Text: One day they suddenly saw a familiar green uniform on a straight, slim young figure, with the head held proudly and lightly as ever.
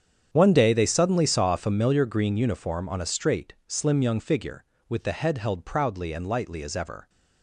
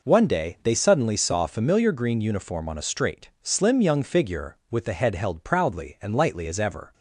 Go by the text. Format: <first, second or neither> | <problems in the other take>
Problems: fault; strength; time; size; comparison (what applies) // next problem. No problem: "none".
second | gets quieter; strong; throughout; 15 dB